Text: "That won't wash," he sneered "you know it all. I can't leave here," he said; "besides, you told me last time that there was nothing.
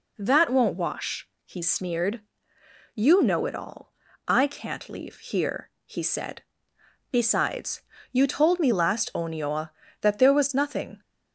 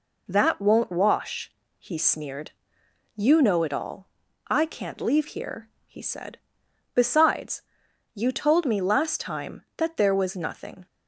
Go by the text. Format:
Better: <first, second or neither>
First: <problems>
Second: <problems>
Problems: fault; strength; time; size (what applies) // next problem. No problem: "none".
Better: second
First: pauses between "sneered" and "you"; noticeable; at 2.2 s; 0.72 s long // says "onioa" for "time"; at 9.1 s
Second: pauses between "sneered" and "you"; noticeable; at 2.5 s; 0.62 s long